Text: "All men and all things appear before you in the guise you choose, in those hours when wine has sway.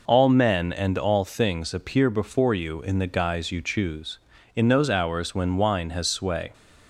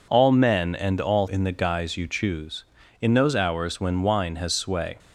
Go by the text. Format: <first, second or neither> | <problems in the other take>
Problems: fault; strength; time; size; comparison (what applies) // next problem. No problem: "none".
first | skips "things appear before you"; at 1.2 s